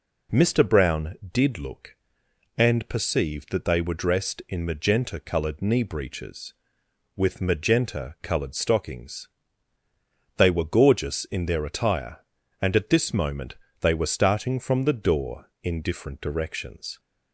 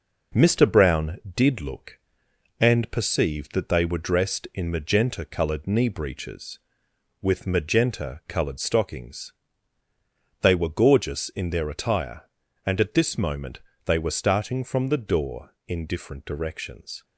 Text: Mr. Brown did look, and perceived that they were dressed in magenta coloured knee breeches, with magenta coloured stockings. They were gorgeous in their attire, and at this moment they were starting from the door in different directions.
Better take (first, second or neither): first